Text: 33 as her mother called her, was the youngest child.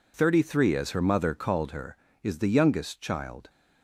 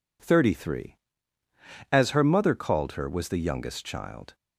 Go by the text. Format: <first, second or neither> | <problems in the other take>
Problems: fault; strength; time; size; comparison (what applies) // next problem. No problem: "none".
second | says "is" for "was"; at 2.2 s